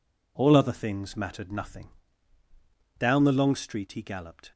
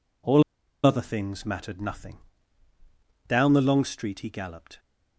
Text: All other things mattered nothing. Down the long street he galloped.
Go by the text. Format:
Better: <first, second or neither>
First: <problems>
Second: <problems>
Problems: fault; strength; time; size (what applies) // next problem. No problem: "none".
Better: first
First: none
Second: pauses between "All" and "other"; at 0.4 s; 0.41 s long